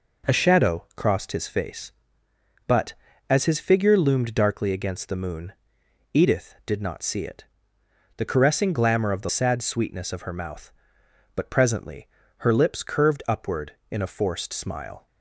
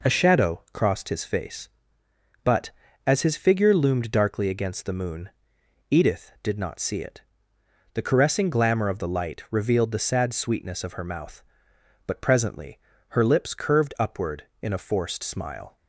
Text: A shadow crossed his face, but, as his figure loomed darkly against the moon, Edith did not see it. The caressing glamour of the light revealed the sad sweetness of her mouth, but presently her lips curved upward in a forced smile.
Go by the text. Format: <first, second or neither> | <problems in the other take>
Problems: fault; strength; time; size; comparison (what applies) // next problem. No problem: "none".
second | skips "light revealed the"; at 9.2 s // pauses between "presently" and "her"; slight; at 12.0 s; 0.30 s long; slight in the second